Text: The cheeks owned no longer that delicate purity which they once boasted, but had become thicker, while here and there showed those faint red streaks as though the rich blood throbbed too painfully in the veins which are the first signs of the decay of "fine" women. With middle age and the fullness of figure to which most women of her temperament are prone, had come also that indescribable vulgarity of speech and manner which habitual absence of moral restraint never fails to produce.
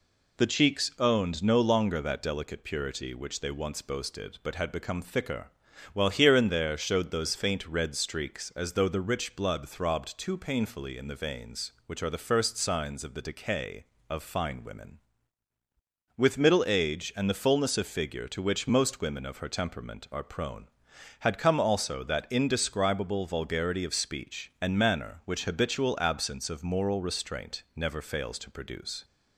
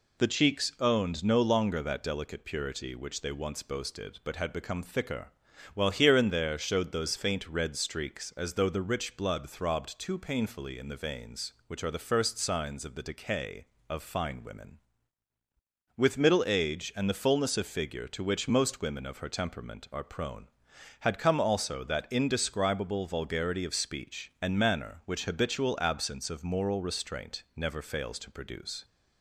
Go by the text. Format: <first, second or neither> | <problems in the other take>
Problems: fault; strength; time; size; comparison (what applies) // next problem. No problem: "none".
neither | none